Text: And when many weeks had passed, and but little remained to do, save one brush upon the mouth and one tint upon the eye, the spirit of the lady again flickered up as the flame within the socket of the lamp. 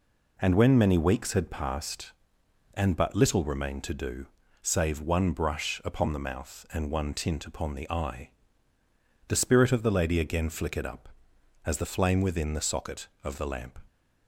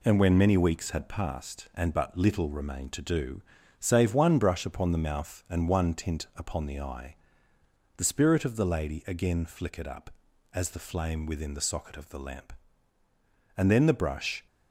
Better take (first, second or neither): first